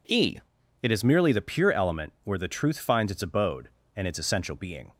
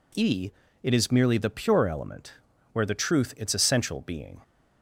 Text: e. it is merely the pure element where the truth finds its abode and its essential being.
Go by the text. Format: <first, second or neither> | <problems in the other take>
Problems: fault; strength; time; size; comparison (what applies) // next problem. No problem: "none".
first | pauses between "element" and "where"; at 2.3 s; 0.38 s long // skips "finds its abode and"; at 3.3 s